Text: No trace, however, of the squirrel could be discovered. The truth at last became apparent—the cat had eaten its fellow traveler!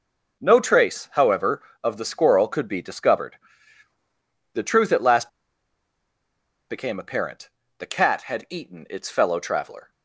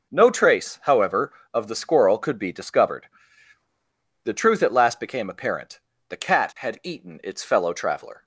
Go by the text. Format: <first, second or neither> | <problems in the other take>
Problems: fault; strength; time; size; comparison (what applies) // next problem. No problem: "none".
second | pauses between "last" and "became"; strong; at 5.2 s; 1.4 s long